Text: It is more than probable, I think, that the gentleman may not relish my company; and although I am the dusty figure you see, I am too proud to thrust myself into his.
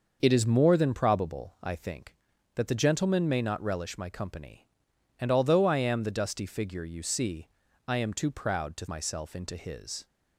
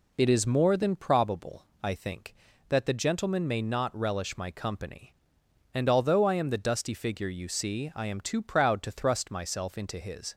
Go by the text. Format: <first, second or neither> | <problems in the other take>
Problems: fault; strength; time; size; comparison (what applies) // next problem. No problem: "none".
second | starts louder than the rest; noticeable; until 1.2 s; 6 dB // skips "thrust"; at 8.8 s